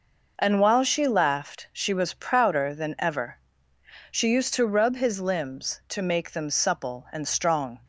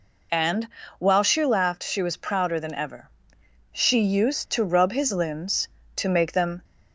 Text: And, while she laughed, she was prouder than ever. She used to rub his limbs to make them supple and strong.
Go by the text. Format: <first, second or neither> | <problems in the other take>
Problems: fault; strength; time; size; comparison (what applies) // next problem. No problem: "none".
first | stops before "supple and strong"; at 6.6 s